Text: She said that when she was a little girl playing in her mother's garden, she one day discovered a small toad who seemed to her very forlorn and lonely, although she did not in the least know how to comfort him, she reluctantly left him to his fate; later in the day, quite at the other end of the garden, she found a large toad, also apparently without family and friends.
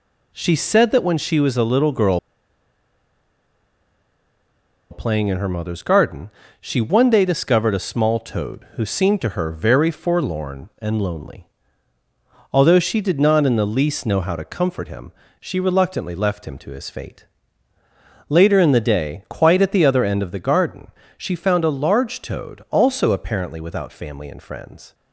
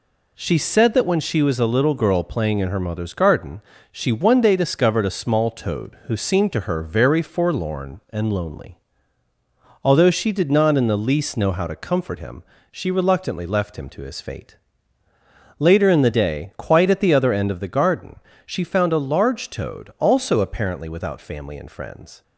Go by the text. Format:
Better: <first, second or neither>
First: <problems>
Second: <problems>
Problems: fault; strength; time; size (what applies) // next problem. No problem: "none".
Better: second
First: pauses between "girl" and "playing"; strong; at 2.1 s; 2.7 s long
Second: none